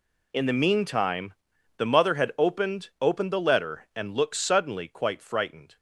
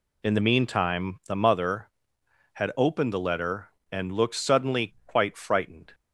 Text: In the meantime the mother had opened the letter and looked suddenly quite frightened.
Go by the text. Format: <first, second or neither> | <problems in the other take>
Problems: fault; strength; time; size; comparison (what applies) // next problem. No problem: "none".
second | pauses between "meantime" and "the"; at 1.3 s; 0.42 s long // says "opened" twice; at 3.0 s